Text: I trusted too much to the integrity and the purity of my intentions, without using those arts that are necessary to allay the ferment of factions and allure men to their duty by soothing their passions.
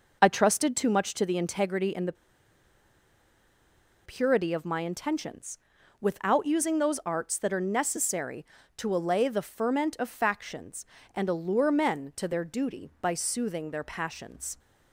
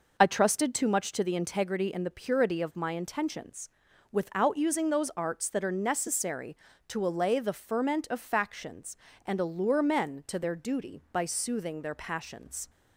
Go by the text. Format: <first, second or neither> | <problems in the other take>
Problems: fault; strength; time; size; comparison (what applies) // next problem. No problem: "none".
second | pauses between "the" and "purity"; strong; at 2.1 s; 1.9 s long